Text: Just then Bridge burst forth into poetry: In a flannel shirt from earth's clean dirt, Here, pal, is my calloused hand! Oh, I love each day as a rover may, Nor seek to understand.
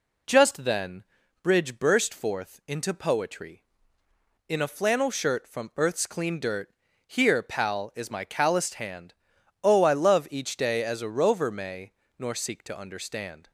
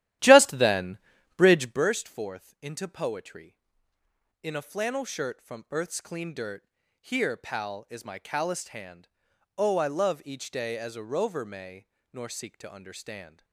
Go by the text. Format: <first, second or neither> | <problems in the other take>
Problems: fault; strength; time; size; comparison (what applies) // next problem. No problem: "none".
first | starts louder than the rest; strong; until 1.9 s; 13 dB // pauses between "then" and "Bridge"; at 0.9 s; 0.38 s long; also in the first